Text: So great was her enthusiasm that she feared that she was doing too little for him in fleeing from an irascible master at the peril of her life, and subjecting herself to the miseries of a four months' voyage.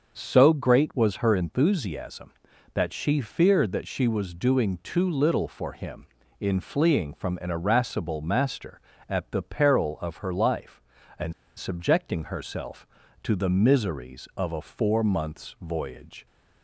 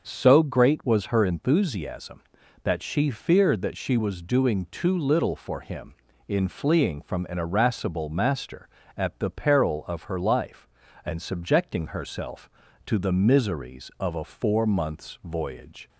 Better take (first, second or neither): second